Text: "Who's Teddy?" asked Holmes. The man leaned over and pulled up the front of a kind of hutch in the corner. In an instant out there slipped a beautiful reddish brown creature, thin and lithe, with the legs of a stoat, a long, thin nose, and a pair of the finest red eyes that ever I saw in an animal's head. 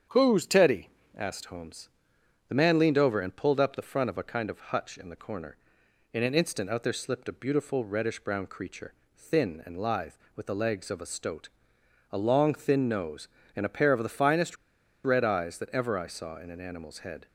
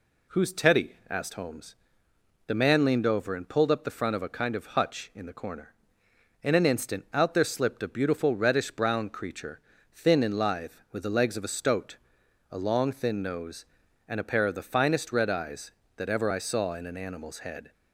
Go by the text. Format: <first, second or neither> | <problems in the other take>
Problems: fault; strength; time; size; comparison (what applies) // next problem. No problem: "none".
second | starts louder than the rest; strong; until 1.3 s; 8 dB // pauses between "finest" and "red"; noticeable; at 14.5 s; 0.49 s long